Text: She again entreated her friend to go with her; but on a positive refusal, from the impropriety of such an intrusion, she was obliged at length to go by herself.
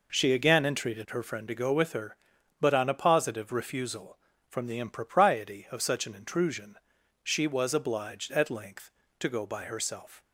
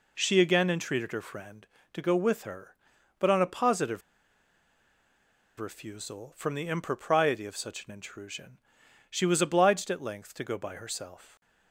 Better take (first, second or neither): first